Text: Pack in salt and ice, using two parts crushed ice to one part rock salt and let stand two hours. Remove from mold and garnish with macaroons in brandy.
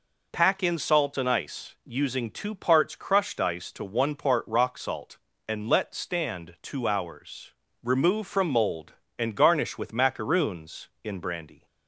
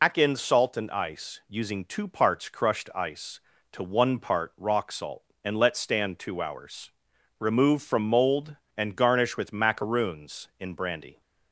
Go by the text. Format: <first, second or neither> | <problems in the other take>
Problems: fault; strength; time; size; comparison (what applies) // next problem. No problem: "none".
first | loses the start of "Pack"; at 0.0 s; 105 ms